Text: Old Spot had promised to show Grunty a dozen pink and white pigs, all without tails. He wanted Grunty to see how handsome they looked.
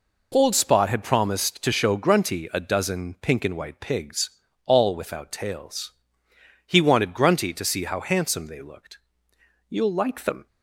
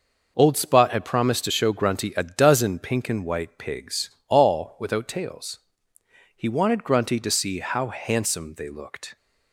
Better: second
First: goes on to say "You'll like them"; noticeable; from 9.6 s on; 0.78 s long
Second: none

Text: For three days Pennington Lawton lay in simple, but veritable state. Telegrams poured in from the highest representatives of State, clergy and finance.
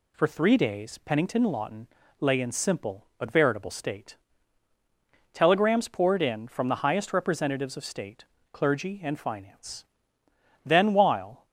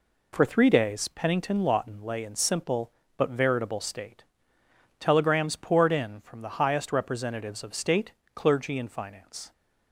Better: second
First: pauses between "Lawton" and "lay"; slight; at 1.8 s; 0.34 s long // goes on to say "Then while"; noticeable; from 10.6 s on; 0.80 s long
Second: none

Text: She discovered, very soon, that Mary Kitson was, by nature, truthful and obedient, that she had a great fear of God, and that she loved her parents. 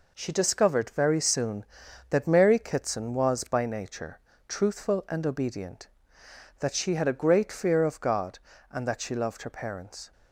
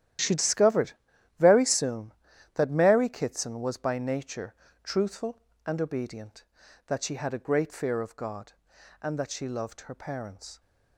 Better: first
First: none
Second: gets quieter; strong; throughout; 14 dB

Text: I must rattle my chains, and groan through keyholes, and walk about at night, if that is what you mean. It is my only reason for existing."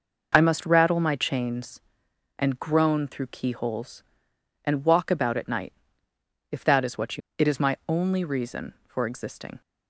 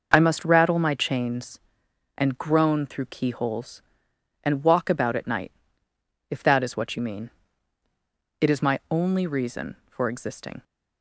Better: second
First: skips "mean"; at 7.2 s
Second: none

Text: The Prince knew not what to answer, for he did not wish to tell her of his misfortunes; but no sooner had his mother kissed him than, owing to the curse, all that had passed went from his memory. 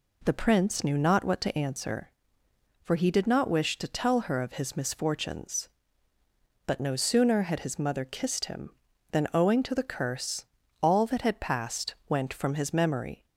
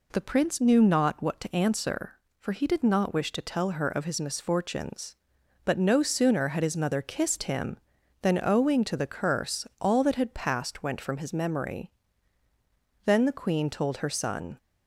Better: first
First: none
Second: goes on to say "Then the Queen told her son"; from 13.0 s on; 1.5 s long

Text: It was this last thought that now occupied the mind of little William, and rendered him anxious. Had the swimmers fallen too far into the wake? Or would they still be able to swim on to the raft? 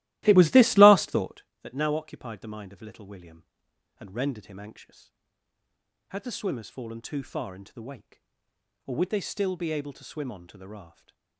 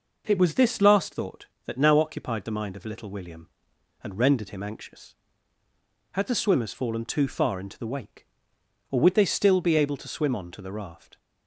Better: second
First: starts louder than the rest; strong; until 1.5 s; 16.5 dB // stays silent after the last word; slight; from 10.8 s on; 0.5 s long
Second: none

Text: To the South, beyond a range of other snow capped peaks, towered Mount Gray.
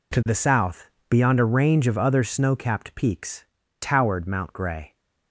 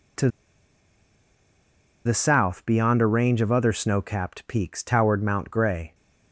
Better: first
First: none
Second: pauses between "To" and "the"; strong; at 0.2 s; 1.7 s long

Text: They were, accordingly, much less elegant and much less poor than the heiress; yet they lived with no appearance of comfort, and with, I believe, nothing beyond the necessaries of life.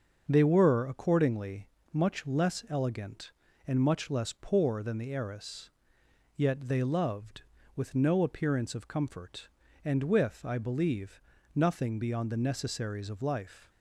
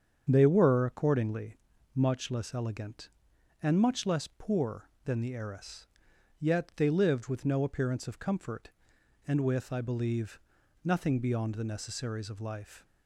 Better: second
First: starts louder than the rest; until 1.2 s; 6.5 dB // says "loved" for "lived"; at 6.8 s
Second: starts louder than the rest; strong; until 1.3 s; 7.5 dB

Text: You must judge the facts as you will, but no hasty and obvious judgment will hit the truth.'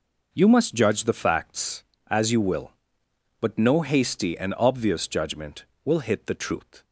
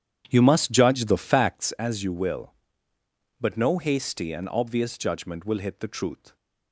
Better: first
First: none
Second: starts louder than the rest; strong; until 1.7 s; 9.5 dB

